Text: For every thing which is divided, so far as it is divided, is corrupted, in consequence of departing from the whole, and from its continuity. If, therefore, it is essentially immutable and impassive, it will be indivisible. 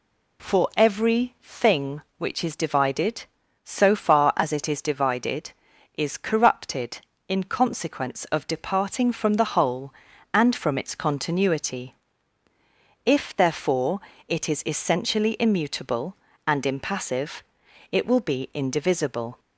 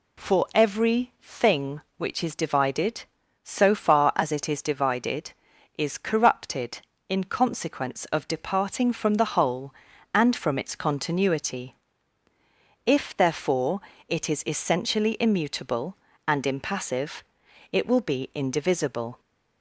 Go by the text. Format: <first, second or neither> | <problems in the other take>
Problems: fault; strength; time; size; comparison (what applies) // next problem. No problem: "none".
neither | none